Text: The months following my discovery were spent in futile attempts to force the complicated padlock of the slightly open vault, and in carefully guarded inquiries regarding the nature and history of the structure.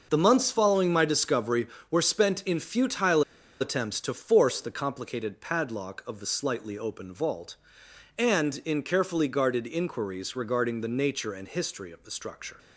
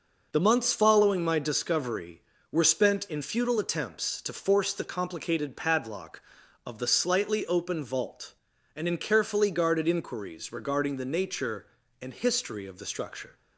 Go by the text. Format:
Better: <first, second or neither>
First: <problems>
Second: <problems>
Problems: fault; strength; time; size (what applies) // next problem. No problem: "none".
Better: second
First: starts louder than the rest; noticeable; until 1.1 s; 6 dB // pauses between "futile" and "attempts"; at 3.2 s; 0.38 s long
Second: none